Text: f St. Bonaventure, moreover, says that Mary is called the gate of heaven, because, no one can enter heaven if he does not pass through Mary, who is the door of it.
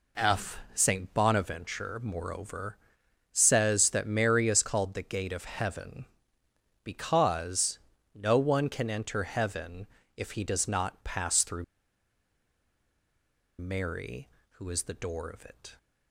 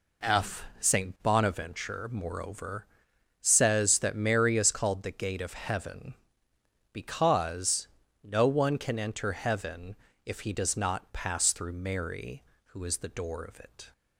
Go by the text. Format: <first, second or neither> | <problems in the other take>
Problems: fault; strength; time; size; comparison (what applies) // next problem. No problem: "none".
second | pauses between "heaven" and "if"; slight; at 9.8 s; 0.30 s long; slight in the second // pauses between "through" and "Mary"; strong; at 11.6 s; 1.9 s long